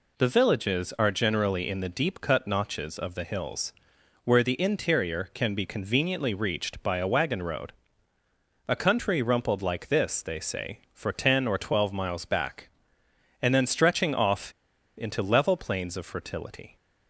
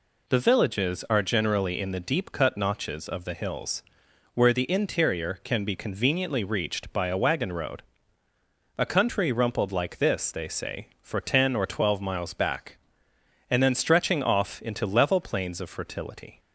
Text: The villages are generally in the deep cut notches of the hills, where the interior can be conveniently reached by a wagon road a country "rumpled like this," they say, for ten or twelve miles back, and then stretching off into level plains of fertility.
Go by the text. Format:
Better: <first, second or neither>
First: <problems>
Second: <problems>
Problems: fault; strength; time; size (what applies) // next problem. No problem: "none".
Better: second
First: pauses between "road" and "a"; noticeable; at 7.7 s; 0.94 s long // pauses between "off" and "into"; at 14.5 s; 0.45 s long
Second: pauses between "road" and "a"; noticeable; at 7.8 s; 0.94 s long